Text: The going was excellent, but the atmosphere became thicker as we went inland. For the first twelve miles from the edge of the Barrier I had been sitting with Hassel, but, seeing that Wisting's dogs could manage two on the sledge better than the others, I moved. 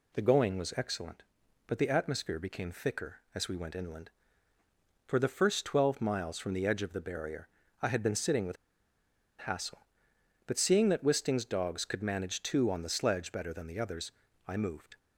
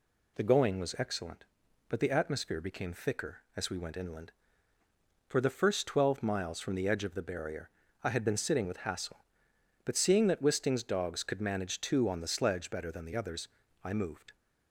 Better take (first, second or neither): second